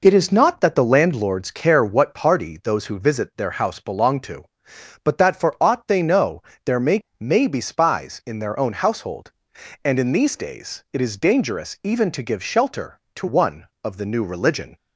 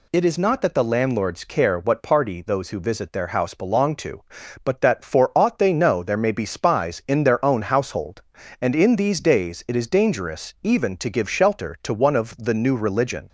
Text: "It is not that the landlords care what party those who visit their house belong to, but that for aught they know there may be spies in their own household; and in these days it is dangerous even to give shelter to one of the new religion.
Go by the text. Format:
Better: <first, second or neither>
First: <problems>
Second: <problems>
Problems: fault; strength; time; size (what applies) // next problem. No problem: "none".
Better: second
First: pauses between "know" and "there"; slight; at 6.4 s; 0.24 s long // says "may" twice; at 7.2 s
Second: none